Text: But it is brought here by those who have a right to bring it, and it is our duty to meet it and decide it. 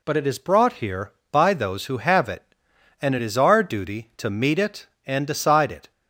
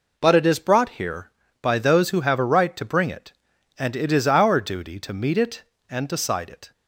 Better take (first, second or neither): second